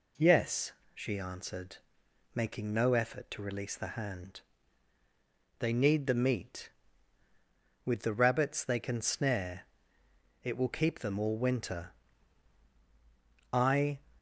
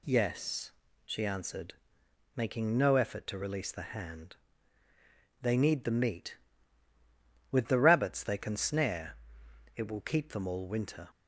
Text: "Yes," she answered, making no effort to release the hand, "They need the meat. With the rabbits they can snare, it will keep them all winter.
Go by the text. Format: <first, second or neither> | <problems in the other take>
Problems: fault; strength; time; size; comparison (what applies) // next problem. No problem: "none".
second | goes on to say "I"; slight; from 13.5 s on; 0.48 s long